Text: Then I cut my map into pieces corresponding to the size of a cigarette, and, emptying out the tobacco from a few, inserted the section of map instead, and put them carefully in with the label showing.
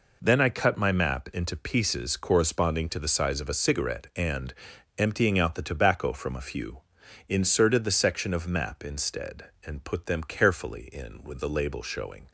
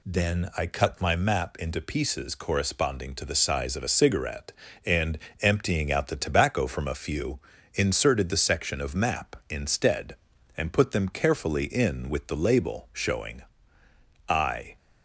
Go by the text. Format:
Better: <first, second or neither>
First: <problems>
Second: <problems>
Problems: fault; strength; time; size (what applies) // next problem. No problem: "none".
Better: first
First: none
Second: goes on to say "I"; slight; from 14.2 s on; 0.48 s long